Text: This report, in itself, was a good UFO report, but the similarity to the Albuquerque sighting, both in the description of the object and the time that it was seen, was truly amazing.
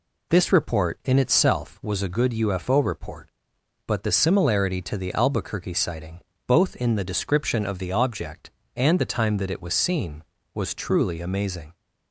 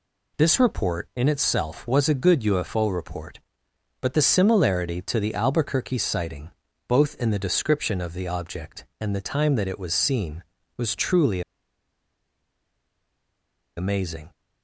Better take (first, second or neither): first